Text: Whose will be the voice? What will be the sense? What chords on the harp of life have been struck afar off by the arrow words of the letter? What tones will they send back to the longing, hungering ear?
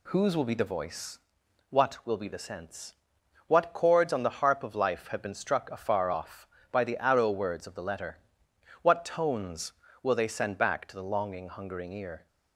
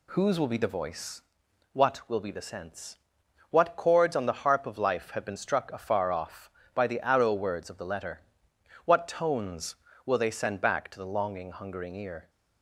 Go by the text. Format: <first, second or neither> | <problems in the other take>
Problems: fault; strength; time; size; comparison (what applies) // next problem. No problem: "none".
neither | none